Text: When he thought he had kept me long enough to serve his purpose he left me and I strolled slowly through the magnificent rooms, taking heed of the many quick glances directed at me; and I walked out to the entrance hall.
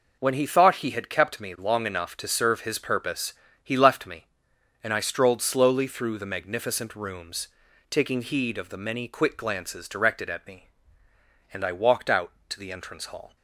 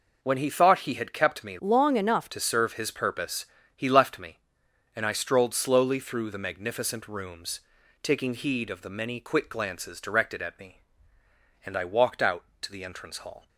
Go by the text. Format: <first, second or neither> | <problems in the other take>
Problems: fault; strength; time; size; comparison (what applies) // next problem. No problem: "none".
first | changes voice from "long" to "enough"; from 1.5 to 2.2 s; 0.7 s long // pauses between "purpose" and "he"; slight; at 3.4 s; 0.30 s long; slight in the first